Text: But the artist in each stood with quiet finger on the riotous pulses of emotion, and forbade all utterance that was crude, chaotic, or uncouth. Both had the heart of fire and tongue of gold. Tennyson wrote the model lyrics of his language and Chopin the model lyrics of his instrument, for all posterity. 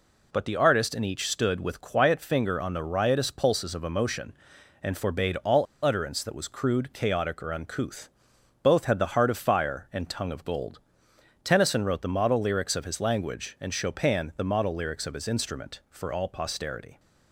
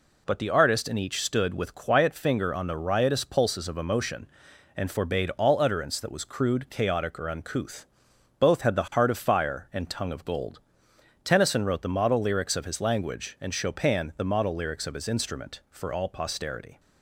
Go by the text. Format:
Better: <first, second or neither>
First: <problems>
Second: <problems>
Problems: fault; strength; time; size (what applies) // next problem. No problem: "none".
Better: second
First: pauses between "all" and "utterance"; slight; at 5.6 s; 0.19 s long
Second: none